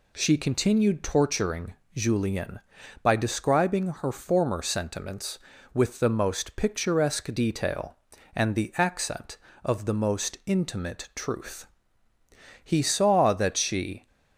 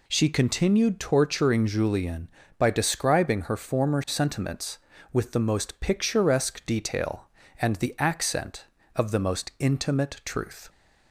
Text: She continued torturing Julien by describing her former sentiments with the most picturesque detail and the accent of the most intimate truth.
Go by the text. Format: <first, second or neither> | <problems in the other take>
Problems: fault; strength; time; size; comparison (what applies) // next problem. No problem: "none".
second | pauses between "torturing" and "Julien"; slight; at 1.7 s; 0.20 s long // goes on to say "He saw that she"; from 12.6 s on; 1.4 s long